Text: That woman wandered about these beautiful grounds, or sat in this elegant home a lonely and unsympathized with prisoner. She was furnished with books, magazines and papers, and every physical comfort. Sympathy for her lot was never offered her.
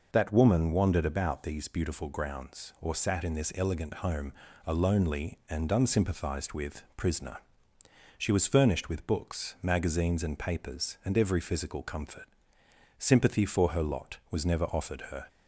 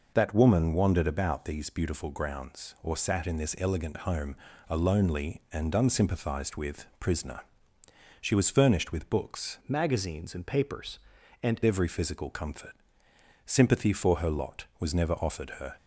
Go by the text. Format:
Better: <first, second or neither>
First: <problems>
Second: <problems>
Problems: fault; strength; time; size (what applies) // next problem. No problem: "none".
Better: first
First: pauses between "home" and "a"; slight; at 4.3 s; 0.30 s long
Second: pauses between "home" and "a"; slight; at 4.3 s; 0.30 s long // changes voice from "magazines" to "and"; from 9.6 to 11.5 s; 1.9 s long